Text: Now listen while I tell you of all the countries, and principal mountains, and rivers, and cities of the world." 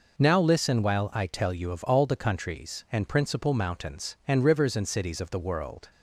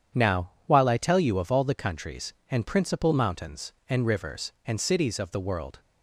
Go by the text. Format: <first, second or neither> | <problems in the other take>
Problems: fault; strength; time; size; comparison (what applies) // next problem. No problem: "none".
first | starts louder than the rest; strong; until 1.2 s; 8.5 dB // skips "listen"; at 0.5 s